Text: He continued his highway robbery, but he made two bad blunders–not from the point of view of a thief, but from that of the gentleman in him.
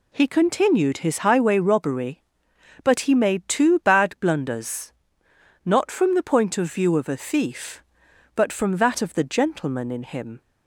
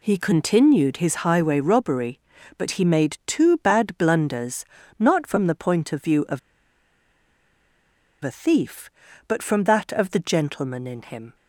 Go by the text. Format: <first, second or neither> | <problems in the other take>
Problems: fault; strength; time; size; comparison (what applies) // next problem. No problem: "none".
first | pauses between "of" and "a"; strong; at 6.3 s; 1.8 s long